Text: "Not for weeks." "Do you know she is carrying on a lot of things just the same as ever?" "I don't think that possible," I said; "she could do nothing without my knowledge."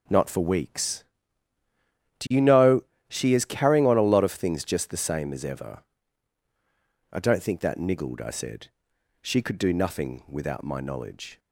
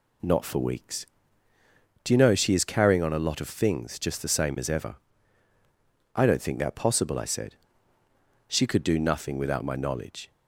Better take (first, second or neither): second